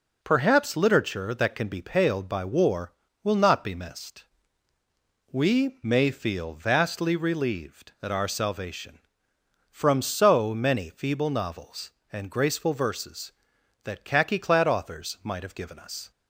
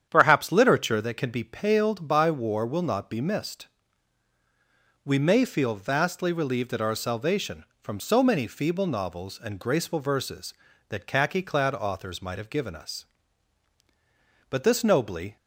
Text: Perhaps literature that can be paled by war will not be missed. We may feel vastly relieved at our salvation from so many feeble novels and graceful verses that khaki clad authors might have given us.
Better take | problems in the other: first | starts louder than the rest; strong; until 1.1 s; 9 dB // goes on to say "But this nobly"; noticeable; from 14.5 s on; 0.86 s long

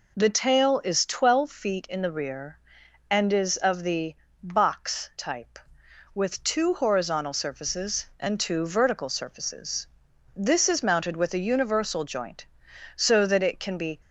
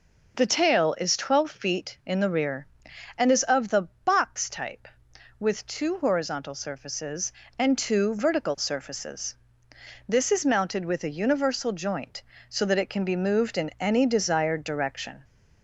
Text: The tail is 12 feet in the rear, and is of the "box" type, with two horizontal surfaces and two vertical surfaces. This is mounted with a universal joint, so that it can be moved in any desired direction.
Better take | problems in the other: second | pauses between "the" and "box"; slight; at 4.1 s; 0.30 s long; slight in the second // stops before "moved in any desired direction"; at 14.0 s

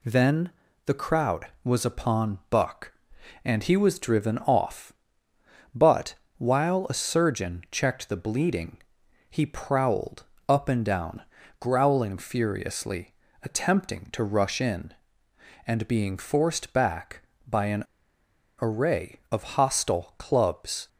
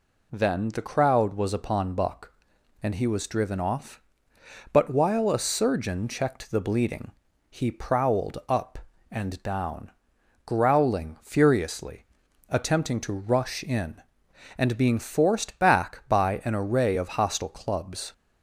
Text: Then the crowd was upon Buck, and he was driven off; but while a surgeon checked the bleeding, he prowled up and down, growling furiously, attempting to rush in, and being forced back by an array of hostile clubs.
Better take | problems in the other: second | pauses between "Then" and "the"; slight; at 0.4 s; 0.36 s long // pauses between "but" and "while"; slight; at 6.1 s; 0.22 s long // pauses between "prowled" and "up"; slight; at 10.2 s; 0.24 s long // pauses between "an" and "array"; noticeable; at 17.8 s; 0.76 s long

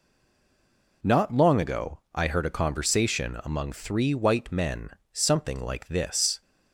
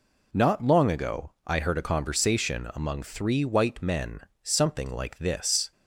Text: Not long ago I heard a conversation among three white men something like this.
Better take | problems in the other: second | stays silent before the first word; until 1.0 s; 1.0 s long // pauses between "ago" and "I"; slight; at 1.9 s; 0.16 s long; slight in the second // pauses between "men" and "something"; slight; at 4.8 s; 0.24 s long; slight in the second

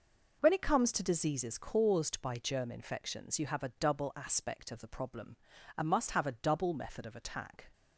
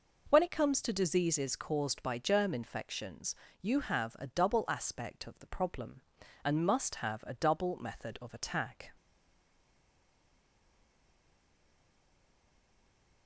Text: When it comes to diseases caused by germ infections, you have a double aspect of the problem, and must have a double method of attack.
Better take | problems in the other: first | stays silent after the last word; strong; from 8.9 s on; 4.3 s long

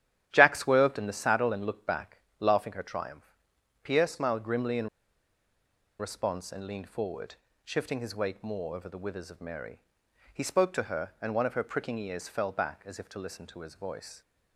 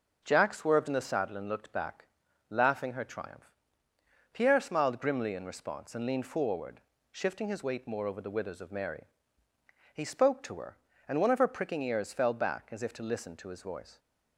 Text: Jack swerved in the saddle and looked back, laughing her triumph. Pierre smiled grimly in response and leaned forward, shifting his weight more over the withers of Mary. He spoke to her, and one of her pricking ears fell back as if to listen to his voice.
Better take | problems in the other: second | starts louder than the rest; strong; until 1.3 s; 11 dB; also in the second // pauses between "in" and "response"; at 4.8 s; 1.1 s long

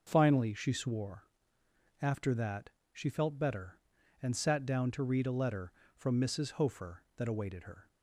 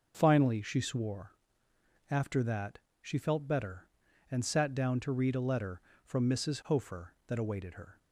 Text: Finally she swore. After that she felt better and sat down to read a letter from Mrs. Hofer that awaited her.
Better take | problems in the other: neither | starts louder than the rest; the same in both // pauses between "that" and "she"; slight; the same in both

